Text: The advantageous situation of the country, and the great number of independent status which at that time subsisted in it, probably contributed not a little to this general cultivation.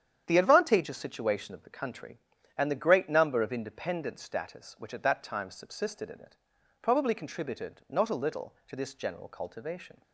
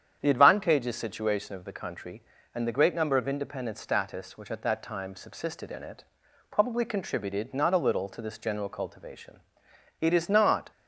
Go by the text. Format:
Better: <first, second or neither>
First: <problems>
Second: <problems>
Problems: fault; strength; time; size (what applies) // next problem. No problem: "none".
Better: first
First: starts louder than the rest; strong; until 1.2 s; 9 dB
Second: starts louder than the rest; strong; until 1.2 s; 8.5 dB // goes on to say "It is not"; noticeable; from 10.0 s on; 0.70 s long